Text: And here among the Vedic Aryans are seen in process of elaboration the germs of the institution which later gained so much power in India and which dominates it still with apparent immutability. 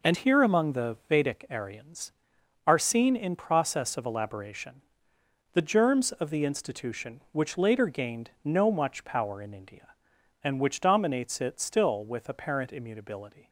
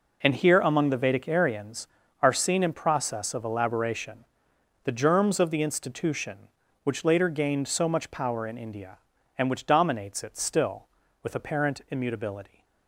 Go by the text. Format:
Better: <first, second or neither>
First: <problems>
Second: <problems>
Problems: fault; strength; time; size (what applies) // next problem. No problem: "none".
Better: second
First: pauses between "elaboration" and "the"; noticeable; at 4.8 s; 0.72 s long // says "no" for "so"; at 8.4 s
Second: pauses between "elaboration" and "the"; noticeable; at 4.2 s; 0.58 s long